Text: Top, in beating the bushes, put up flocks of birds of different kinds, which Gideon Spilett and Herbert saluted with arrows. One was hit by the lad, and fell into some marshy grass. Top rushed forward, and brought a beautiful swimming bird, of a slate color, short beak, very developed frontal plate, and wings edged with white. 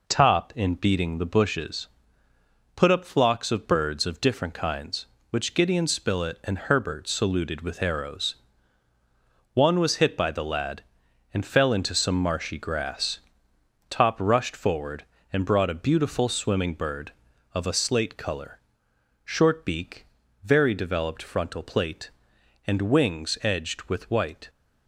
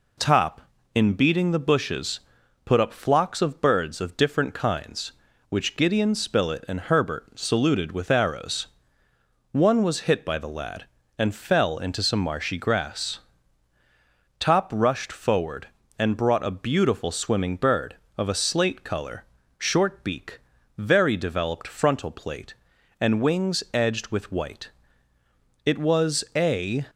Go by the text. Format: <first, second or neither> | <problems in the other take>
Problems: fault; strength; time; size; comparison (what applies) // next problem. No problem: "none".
first | goes on to say "It was a"; noticeable; from 25.6 s on; 1.2 s long